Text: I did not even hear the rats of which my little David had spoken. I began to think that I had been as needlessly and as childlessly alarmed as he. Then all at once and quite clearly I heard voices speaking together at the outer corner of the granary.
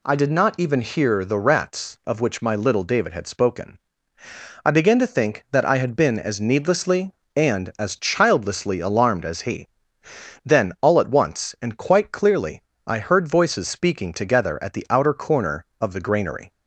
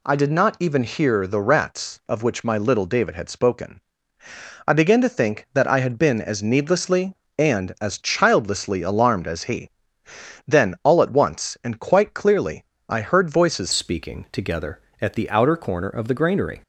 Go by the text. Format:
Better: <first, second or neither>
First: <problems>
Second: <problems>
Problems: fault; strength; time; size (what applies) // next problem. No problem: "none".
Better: first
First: pauses between "clearly" and "I"; slight; at 12.6 s; 0.24 s long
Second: pauses between "clearly" and "I"; slight; at 12.6 s; 0.24 s long // changes voice at "speaking"; from 13.7 s on; 2.9 s long